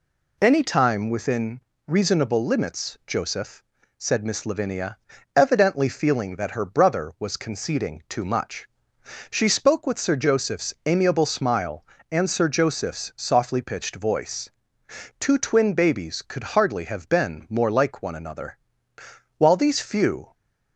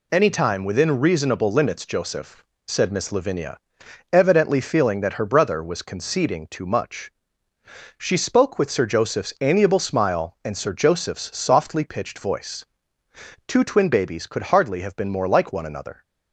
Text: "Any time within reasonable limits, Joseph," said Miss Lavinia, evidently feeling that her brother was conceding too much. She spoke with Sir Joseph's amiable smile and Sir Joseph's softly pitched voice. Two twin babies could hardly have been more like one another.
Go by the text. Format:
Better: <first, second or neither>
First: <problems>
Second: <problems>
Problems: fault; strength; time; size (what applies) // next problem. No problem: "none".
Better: second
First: pauses between "within" and "reasonable"; slight; at 1.6 s; 0.28 s long // goes on to say "While these few"; noticeable; from 19.3 s on; 0.96 s long // stays silent after the last word; slight; from 20.2 s on; 0.5 s long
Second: none